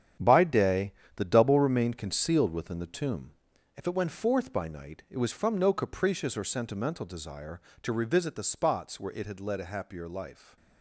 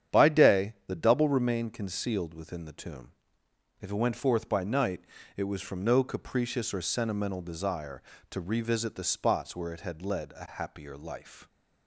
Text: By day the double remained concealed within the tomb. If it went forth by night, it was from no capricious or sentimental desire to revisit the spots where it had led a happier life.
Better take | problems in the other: second | gets quieter; strong; throughout; 9 dB // starts louder than the rest; strong; until 1.4 s; 9 dB; strong in the second // pauses between "day" and "the"; slight; at 0.9 s; 0.20 s long

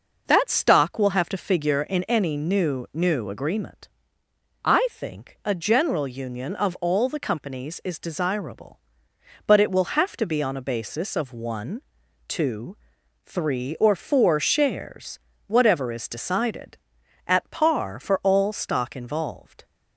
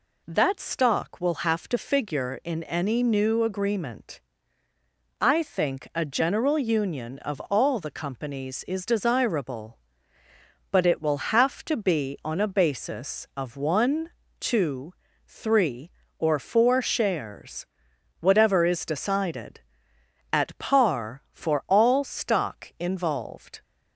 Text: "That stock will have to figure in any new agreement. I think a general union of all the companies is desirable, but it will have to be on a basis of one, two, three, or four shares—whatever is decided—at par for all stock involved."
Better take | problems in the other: second | says "new" twice; at 2.9 s

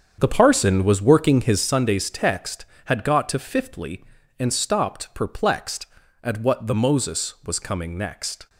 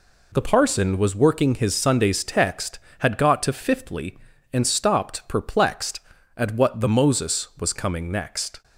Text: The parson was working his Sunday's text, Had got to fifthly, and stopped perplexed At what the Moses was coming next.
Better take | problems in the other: second | starts louder than the rest; strong; until 1.7 s; 7.5 dB

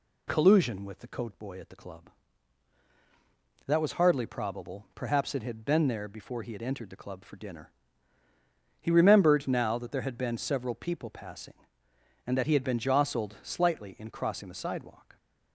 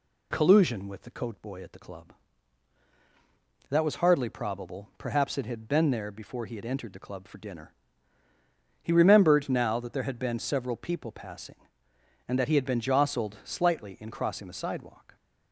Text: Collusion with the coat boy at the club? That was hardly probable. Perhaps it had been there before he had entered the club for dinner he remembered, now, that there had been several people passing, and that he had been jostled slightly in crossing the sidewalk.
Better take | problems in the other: neither | pauses between "dinner" and "he"; the same in both

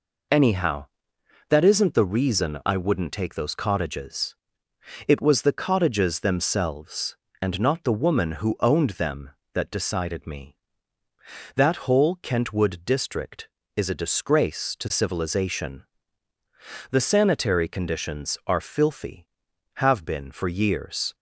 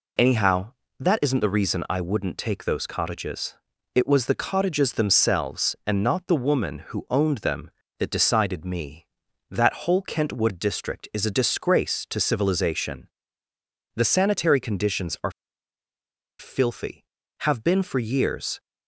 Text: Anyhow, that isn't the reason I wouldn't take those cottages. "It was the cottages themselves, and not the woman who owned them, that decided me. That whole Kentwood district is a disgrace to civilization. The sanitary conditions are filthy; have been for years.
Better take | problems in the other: first | pauses between "are" and "filthy"; at 15.3 s; 1.0 s long

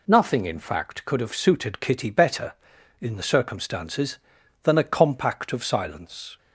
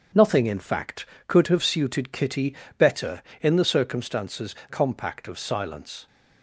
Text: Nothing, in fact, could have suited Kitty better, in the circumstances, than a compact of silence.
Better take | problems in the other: first | pauses between "Kitty" and "better"; slight; at 2.5 s; 0.22 s long // skips "than a"; at 4.6 s

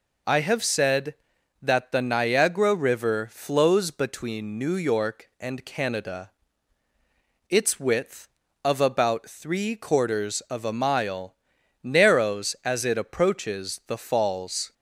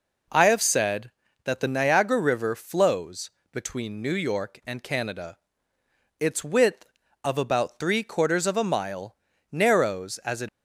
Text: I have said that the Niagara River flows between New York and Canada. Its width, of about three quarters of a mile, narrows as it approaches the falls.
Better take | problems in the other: first | pauses between "flows" and "between"; slight; at 3.2 s; 0.22 s long // stops before "approaches the falls"; at 10.4 s

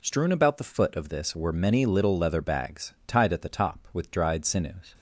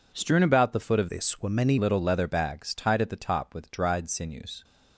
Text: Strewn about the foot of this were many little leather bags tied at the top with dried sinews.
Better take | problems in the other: first | changes voice from "this" to "many"; from 1.0 to 1.7 s; 0.7 s long

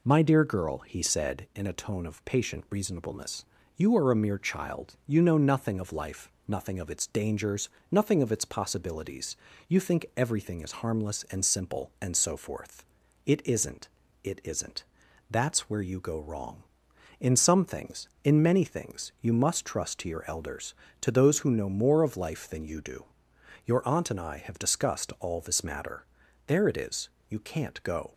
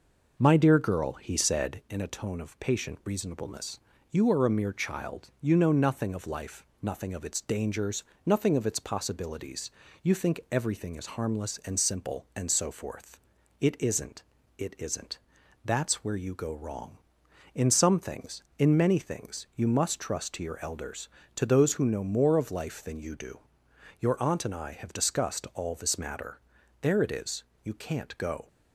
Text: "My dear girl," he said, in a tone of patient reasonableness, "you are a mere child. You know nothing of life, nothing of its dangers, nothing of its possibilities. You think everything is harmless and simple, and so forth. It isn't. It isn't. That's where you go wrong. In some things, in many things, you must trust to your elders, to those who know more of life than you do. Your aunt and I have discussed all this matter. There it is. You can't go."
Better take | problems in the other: first | starts louder than the rest; noticeable; until 2.1 s; 5.5 dB

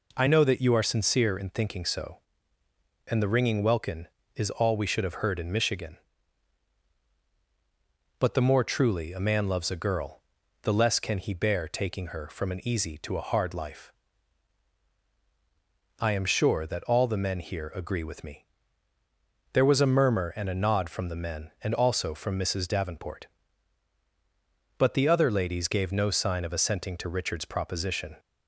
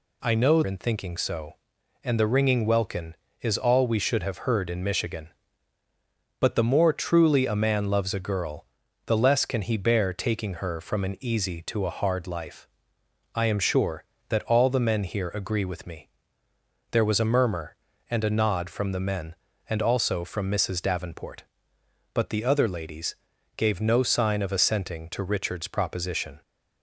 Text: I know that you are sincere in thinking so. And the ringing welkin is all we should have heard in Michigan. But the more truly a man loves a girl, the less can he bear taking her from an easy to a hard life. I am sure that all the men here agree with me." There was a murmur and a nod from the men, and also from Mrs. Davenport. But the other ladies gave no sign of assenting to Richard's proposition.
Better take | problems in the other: first | skips "that you are sincere"; at 0.6 s // pauses between "ladies" and "gave"; at 23.1 s; 0.40 s long

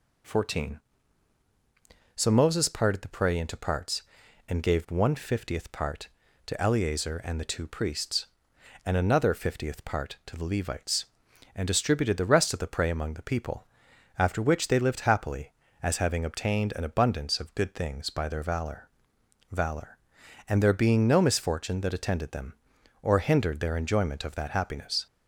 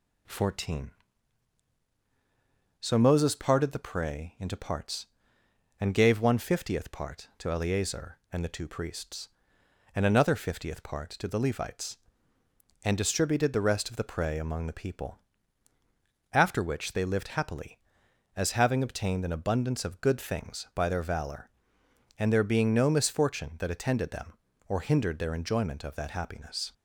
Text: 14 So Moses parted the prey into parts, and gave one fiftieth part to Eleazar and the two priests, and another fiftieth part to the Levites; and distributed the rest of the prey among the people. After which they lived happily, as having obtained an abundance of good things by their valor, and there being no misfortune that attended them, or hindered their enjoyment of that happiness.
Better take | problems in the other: second | says "valor" twice; at 19.5 s

